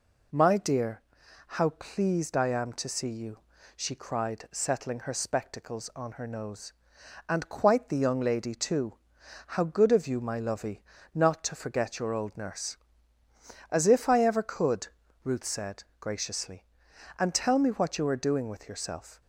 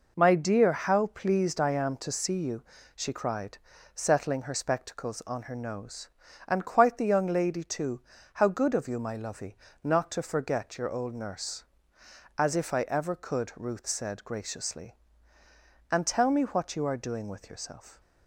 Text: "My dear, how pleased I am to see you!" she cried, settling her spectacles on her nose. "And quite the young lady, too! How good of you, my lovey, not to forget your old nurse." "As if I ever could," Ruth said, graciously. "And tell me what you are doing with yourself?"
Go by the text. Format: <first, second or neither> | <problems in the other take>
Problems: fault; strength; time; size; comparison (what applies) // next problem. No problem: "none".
neither | none